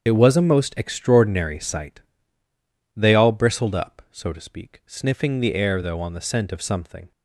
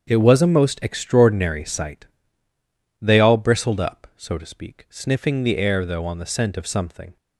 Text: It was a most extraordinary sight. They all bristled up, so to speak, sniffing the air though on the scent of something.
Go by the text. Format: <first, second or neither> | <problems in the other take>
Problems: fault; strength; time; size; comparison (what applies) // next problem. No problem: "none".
second | loses the start of "It"; at 0.0 s; 40 ms // starts louder than the rest; strong; until 1.0 s; 7.5 dB; strong in the second